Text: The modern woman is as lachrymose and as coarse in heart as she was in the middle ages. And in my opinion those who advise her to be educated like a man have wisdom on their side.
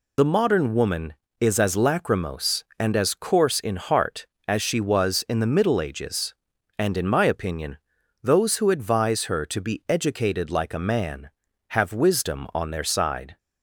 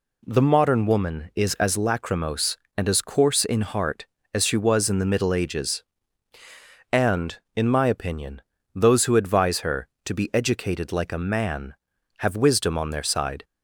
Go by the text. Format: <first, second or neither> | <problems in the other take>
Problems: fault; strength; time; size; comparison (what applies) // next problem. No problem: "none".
second | loses the start of "The"; at 0.1 s; 30 ms // pauses between "opinion" and "those"; at 7.7 s; 0.44 s long; slight in the second